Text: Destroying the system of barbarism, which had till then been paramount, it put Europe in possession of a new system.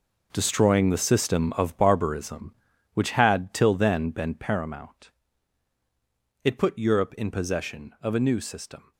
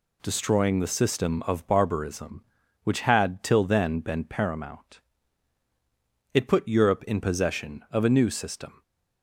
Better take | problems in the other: second | gets quieter; strong; throughout; 12.5 dB

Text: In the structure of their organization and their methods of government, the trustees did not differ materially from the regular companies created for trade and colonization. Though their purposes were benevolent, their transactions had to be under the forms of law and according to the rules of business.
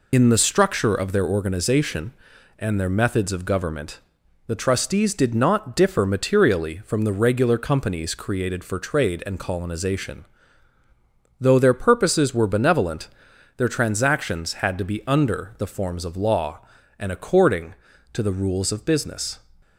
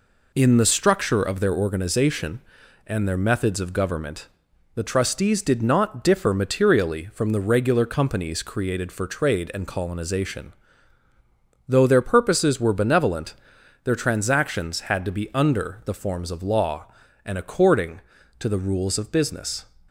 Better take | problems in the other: second | loses the start of "In"; at 0.1 s; 65 ms

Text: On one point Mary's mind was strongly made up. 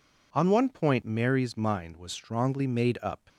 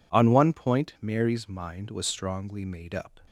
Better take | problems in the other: neither | none

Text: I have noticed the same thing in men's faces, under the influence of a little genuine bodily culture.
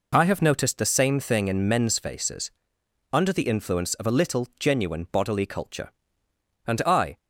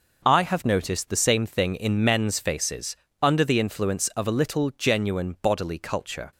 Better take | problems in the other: second | goes on to say "And I"; from 6.6 s on; 0.50 s long

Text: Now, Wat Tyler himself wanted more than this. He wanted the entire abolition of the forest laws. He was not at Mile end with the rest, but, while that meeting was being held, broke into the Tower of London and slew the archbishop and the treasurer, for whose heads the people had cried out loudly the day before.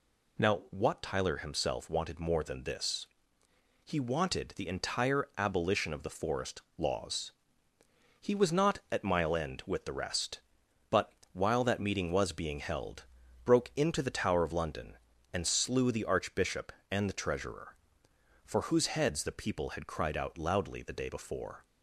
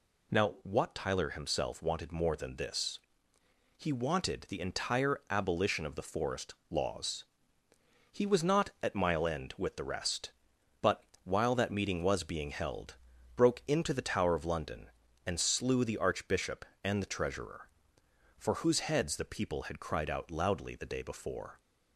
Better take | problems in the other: neither | pauses between "forest" and "laws"; slight; the same in both

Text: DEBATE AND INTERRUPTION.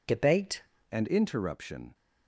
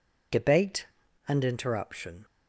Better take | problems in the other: second | changes voice at "AND"; from 0.9 s on; 1.0 s long

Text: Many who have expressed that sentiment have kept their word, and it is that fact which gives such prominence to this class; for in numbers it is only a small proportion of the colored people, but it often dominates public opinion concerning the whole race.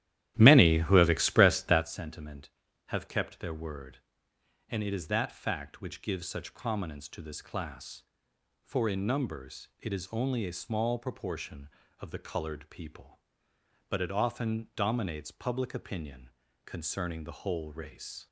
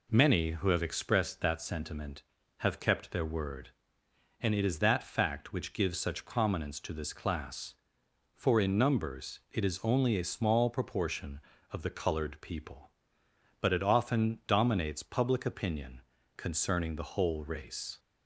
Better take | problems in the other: second | starts louder than the rest; strong; until 2.0 s; 12.5 dB // pauses between "opinion" and "concerning"; slight; at 16.2 s; 0.34 s long; slight in the second

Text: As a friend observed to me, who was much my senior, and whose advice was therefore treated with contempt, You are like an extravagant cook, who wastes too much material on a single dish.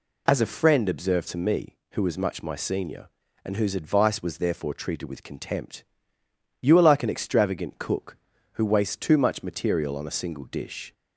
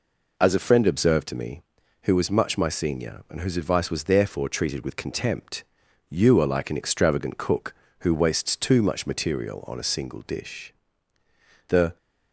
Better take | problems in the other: first | goes on to say "The"; slight; from 11.6 s on; 0.28 s long

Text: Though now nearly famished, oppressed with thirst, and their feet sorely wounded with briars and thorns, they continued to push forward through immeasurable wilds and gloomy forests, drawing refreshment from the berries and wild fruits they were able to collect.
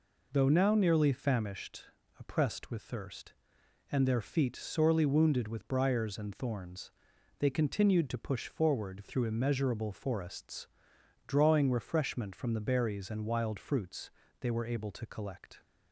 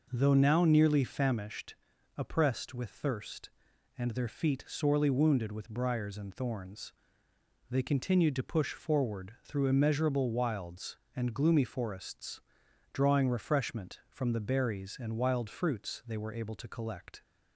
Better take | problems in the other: second | skips "wilds and gloomy"; at 9.9 s // pauses between "fruits" and "they"; slight; at 14.0 s; 0.32 s long

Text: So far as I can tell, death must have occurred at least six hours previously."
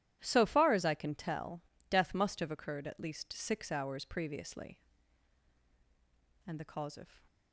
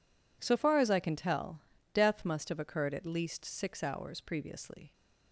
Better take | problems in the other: second | starts louder than the rest; strong; until 1.2 s; 12 dB // goes on to say "And the cause of"; noticeable; from 6.4 s on; 0.76 s long

